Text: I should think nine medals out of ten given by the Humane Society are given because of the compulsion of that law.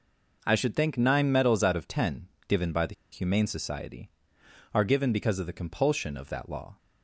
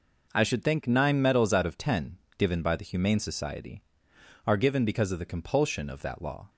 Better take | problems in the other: second | pauses between "ten" and "given"; slight; at 2.2 s; 0.20 s long; slight in the second // pauses between "the" and "Humane"; slight; at 2.9 s; 0.18 s long

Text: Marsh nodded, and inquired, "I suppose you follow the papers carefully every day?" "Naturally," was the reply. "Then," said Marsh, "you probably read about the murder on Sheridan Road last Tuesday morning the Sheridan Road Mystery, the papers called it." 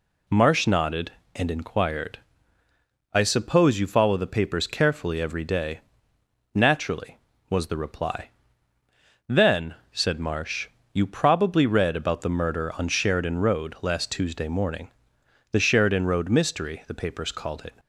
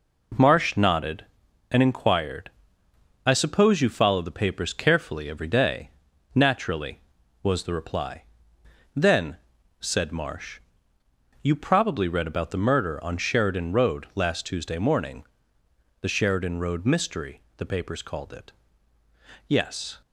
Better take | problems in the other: first | pauses between "morning" and "the"; noticeable; at 15.2 s; 0.74 s long; noticeable in the first // goes on to say "Yes"; from 19.4 s on; 0.52 s long

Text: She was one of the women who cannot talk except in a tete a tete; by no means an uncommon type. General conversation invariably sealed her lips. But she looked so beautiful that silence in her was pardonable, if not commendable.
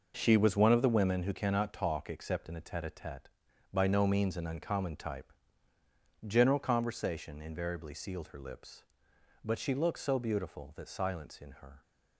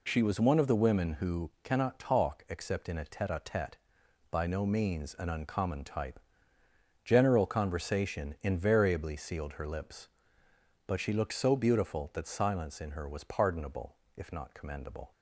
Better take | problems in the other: second | stops before "was pardonable if not commendable"; at 11.8 s

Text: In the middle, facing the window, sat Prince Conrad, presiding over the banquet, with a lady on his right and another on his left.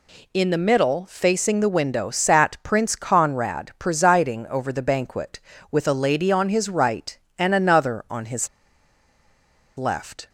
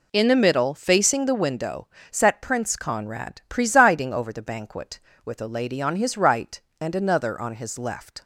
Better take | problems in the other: second | pauses between "his" and "left"; strong; at 8.4 s; 1.3 s long

